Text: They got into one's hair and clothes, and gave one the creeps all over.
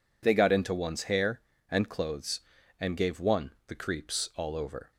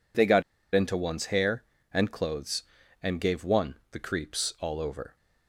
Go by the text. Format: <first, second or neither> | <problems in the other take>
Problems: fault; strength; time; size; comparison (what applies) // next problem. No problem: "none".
first | pauses between "got" and "into"; slight; at 0.4 s; 0.32 s long